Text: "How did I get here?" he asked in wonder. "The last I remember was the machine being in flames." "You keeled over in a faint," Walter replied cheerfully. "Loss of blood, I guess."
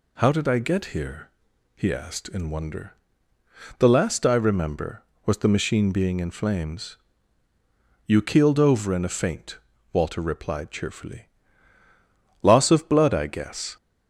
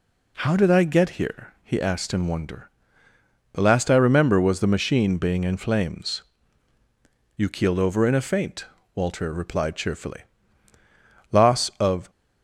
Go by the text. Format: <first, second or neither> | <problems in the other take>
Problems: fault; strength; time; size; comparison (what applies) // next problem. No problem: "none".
first | stops before "blood I guess"; at 12.0 s